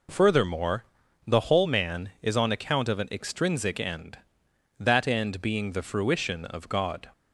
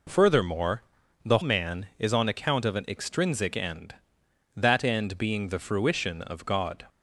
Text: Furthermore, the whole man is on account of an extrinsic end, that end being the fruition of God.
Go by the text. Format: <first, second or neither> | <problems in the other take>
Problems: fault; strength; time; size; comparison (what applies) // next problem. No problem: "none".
first | skips "whole"; at 1.4 s